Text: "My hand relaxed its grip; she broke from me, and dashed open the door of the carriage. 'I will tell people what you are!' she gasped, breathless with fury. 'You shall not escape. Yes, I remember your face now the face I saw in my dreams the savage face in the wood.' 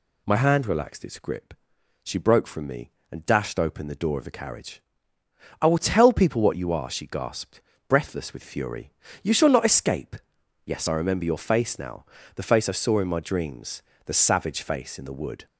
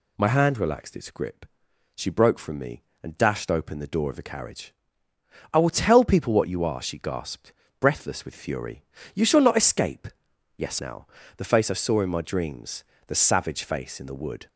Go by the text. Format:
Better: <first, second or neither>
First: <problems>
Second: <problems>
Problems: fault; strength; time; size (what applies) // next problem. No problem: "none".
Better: first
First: pauses between "now" and "the"; slight; at 12.0 s; 0.32 s long // pauses between "dreams" and "the"; slight; at 13.8 s; 0.22 s long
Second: skips "I remember your face"; at 10.7 s // pauses between "now" and "the"; slight; at 11.0 s; 0.32 s long // pauses between "dreams" and "the"; slight; at 12.8 s; 0.22 s long